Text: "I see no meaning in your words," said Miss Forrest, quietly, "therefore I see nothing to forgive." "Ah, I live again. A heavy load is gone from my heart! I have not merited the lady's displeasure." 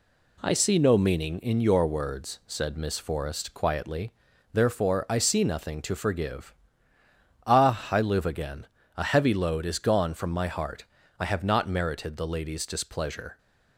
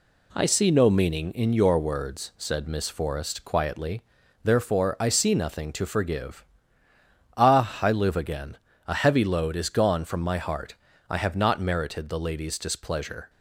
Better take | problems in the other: neither | none

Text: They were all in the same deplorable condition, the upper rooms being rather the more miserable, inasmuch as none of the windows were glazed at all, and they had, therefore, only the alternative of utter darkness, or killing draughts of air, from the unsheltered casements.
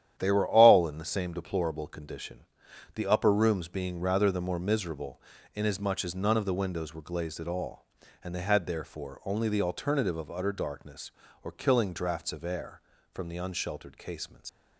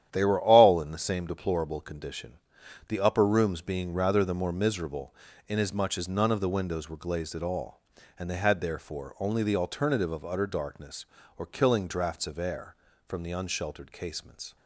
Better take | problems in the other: second | starts louder than the rest; strong; until 1.1 s; 10.5 dB; strong in the second // leaves "casements" unfinished; at 14.4 s; 115 ms

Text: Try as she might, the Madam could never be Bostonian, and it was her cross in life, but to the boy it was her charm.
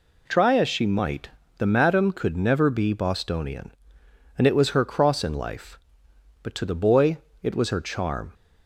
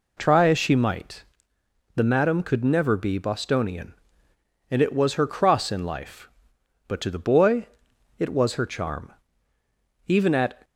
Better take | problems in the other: first | pauses between "boy" and "it"; noticeable; at 7.6 s; 0.50 s long; slight in the first // goes on to say "Even at"; from 10.0 s on; 0.56 s long

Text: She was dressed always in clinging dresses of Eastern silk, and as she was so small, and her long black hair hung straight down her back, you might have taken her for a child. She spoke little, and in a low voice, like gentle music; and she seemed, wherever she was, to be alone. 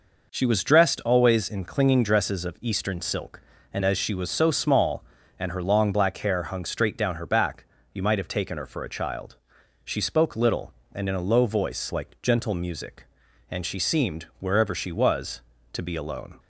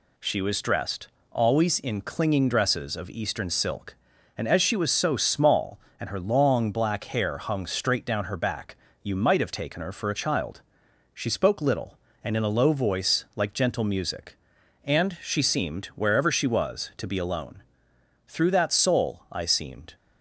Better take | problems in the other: first | pauses between "dressed" and "always"; slight; at 1.0 s; 0.22 s long // goes on to say "Through that soul I seemed"; from 18.2 s on; 1.6 s long

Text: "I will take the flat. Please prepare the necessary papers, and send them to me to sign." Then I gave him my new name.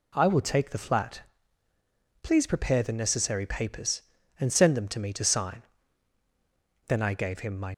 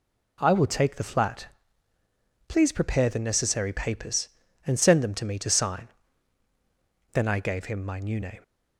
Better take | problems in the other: second | stops before "new name"; at 7.7 s

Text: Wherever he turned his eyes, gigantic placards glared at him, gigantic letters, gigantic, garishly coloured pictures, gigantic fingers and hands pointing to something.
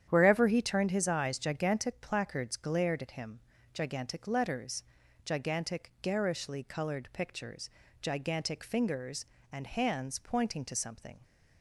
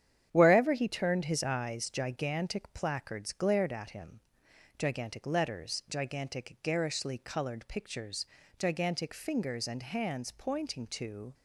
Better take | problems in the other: first | starts louder than the rest; strong; until 1.3 s; 9.5 dB; strong in the first // stops before "something"; at 11.3 s

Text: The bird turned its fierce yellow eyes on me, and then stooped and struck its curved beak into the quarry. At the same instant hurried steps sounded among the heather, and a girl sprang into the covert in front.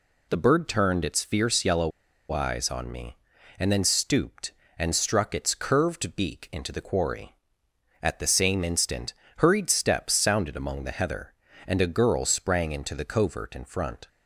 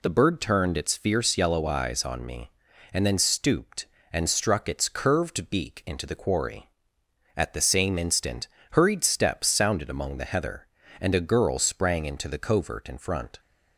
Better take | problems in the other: second | pauses between "yellow" and "eyes"; at 1.9 s; 0.41 s long // pauses between "instant" and "hurried"; slight; at 9.1 s; 0.26 s long; slight in the second

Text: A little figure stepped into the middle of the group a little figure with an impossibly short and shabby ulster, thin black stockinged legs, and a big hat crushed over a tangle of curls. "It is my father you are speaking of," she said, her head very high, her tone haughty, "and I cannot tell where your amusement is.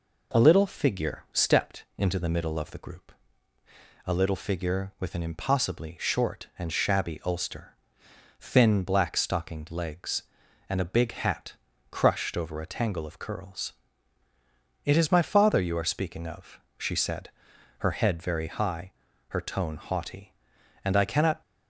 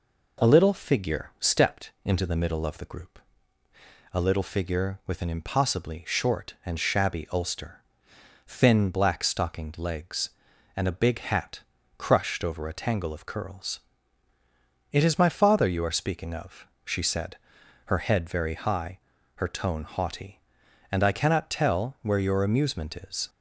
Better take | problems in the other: second | pauses between "group" and "a"; noticeable; at 3.1 s; 0.94 s long; noticeable in the second // pauses between "hat" and "crushed"; at 11.5 s; 0.40 s long; also in the second // stops before "tell where your amusement is"; at 21.4 s

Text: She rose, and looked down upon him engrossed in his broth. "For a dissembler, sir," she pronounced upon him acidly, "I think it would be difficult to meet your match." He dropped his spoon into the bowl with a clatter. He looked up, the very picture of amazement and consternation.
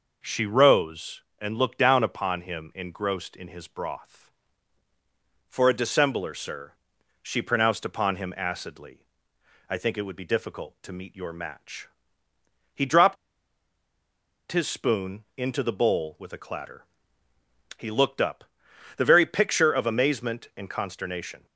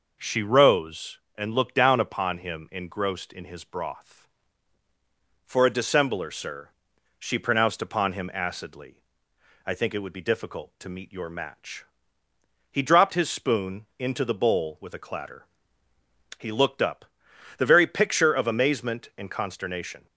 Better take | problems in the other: second | pauses between "dropped" and "his"; strong; at 13.1 s; 1.3 s long

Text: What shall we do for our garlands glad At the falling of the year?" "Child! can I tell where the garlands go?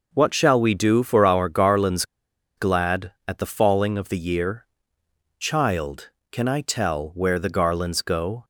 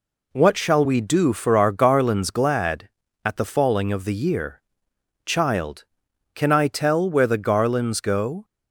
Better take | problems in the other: second | pauses between "garlands" and "glad"; noticeable; at 2.0 s; 0.54 s long

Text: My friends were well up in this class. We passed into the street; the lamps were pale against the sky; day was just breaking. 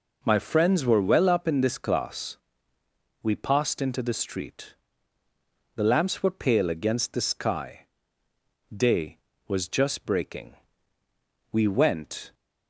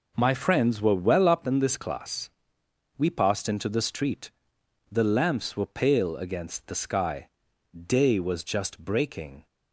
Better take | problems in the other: second | goes on to say "We went"; noticeable; from 11.5 s on; 0.82 s long

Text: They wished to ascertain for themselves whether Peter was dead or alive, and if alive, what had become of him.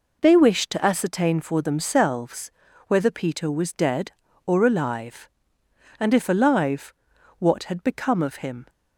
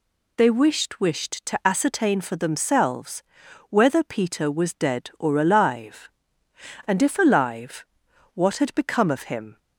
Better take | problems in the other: first | says "wished" twice; at 0.9 s // pauses between "themselves" and "whether"; noticeable; at 3.2 s; 0.48 s long; slight in the first

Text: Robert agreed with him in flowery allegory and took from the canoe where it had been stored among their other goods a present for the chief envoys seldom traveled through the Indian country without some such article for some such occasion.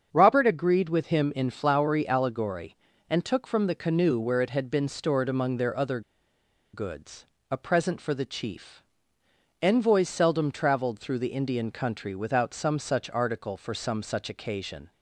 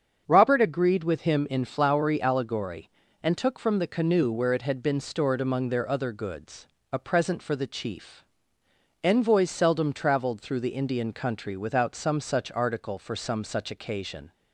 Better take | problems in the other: second | starts louder than the rest; until 1.1 s; 7 dB; also in the second // pauses between "other" and "goods"; noticeable; at 6.0 s; 0.73 s long // pauses between "goods" and "a"; slight; at 7.2 s; 0.24 s long; slight in the second // pauses between "chief" and "envoys"; noticeable; at 8.8 s; 0.80 s long; noticeable in the second

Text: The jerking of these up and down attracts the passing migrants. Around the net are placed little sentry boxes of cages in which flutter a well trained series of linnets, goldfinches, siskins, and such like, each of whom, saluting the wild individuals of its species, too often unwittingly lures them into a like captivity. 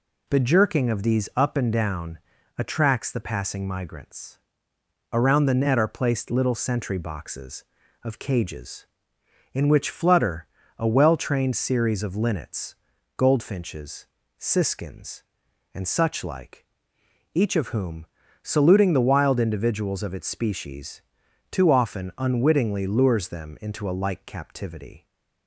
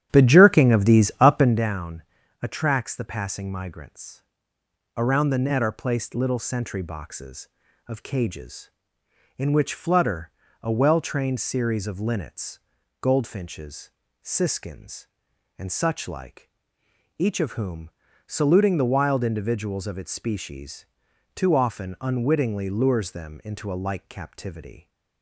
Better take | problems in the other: first | starts louder than the rest; strong; until 1.6 s; 10.5 dB // pauses between "down" and "attracts"; at 2.0 s; 0.40 s long; also in the first // pauses between "flutter" and "a"; slight; at 10.3 s; 0.32 s long; slight in the first

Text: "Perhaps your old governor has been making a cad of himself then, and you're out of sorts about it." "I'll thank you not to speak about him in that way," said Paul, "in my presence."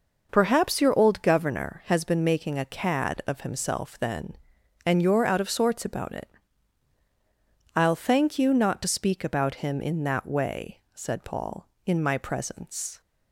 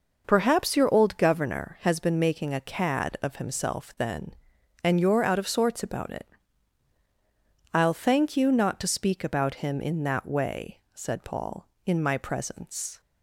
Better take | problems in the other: neither | none

